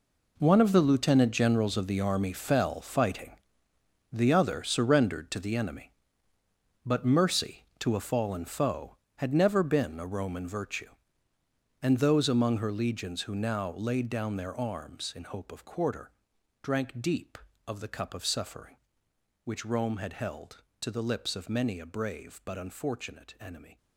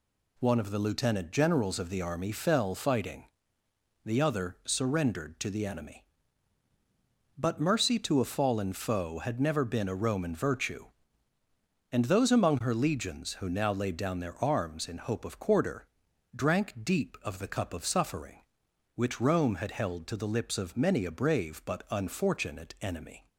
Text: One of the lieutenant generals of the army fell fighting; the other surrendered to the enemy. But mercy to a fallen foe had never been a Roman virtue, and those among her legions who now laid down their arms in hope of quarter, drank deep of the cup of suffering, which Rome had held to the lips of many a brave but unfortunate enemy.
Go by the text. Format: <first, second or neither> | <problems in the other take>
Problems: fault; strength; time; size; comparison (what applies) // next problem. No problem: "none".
second | gets quieter; strong; throughout; 13 dB